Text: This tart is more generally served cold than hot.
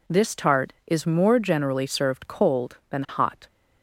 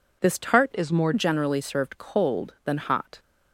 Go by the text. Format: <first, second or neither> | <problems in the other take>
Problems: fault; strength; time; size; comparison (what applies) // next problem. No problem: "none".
first | changes voice from "is" to "more"; from 0.7 to 1.1 s; 0.4 s long